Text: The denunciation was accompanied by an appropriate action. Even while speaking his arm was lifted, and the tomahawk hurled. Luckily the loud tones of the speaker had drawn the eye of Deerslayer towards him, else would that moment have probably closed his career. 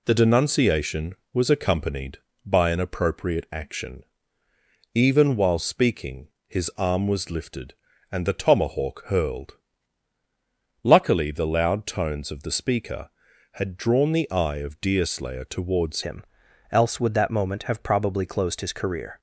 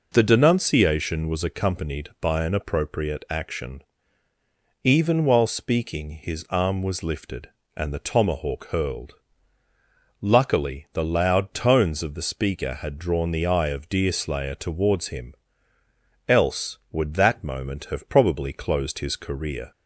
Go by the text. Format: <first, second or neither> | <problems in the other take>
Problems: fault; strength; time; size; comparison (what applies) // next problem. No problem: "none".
second | pauses between "speaking" and "his"; slight; at 6.2 s; 0.20 s long // changes voice at "him"; from 16.0 s on; 3.1 s long